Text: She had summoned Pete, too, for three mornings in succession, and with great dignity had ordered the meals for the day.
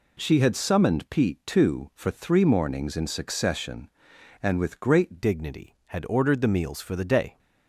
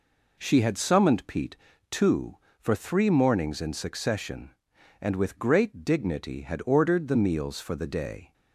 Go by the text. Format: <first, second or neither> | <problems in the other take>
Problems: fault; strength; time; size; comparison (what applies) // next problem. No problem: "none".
second | changes voice at "dignity"; from 5.2 s on; 2.1 s long